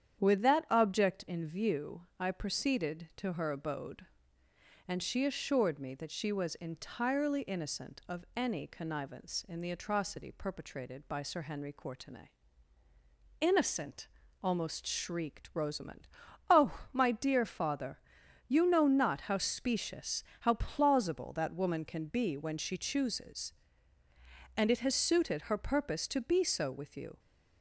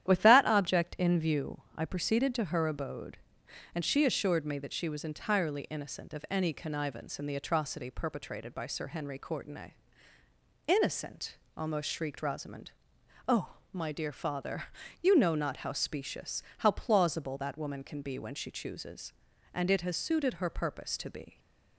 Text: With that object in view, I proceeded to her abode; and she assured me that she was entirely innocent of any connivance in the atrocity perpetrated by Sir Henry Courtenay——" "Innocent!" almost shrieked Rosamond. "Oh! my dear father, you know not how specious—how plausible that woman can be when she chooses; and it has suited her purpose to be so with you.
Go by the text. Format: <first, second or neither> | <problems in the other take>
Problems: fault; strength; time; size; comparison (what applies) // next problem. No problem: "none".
first | starts louder than the rest; strong; until 1.1 s; 11 dB; strong in the first // stops before "so with you"; at 21.3 s